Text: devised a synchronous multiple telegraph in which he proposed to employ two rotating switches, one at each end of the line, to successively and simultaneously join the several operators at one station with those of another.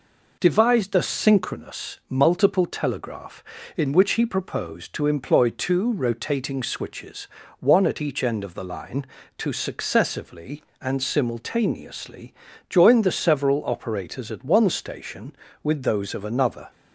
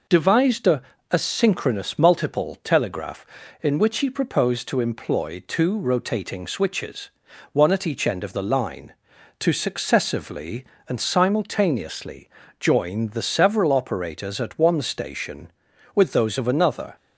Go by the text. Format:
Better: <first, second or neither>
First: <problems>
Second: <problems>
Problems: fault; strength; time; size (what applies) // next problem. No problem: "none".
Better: first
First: pauses between "simultaneously" and "join"; slight; at 12.3 s; 0.34 s long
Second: says "a" twice; at 1.1 s // pauses between "simultaneously" and "join"; slight; at 12.2 s; 0.32 s long